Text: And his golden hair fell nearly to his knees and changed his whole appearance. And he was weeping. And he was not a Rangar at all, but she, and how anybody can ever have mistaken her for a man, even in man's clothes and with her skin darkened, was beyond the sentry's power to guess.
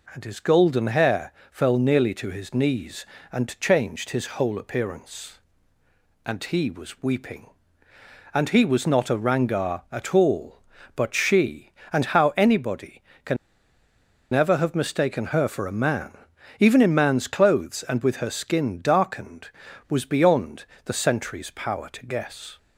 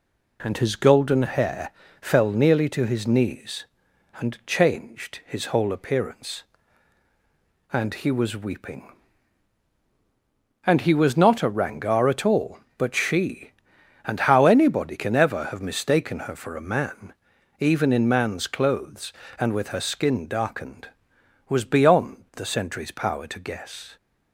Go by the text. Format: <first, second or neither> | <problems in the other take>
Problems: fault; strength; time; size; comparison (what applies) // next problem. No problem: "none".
second | pauses between "hair" and "fell"; slight; at 1.3 s; 0.20 s long; slight in the second // pauses between "can" and "ever"; noticeable; at 13.3 s; 0.97 s long // pauses between "beyond" and "the"; slight; at 20.6 s; 0.18 s long